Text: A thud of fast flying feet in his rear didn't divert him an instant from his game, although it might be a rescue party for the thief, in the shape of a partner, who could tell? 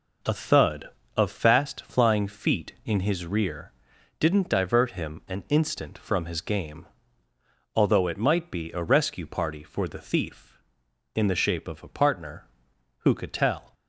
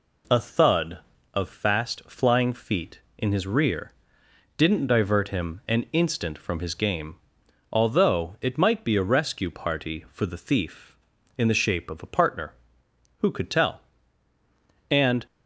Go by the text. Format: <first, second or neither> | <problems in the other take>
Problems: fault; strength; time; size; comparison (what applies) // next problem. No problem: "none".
first | pauses between "rear" and "didn't"; noticeable; at 3.9 s; 0.66 s long; noticeable in the first // goes on to say "And"; slight; from 14.8 s on; 0.36 s long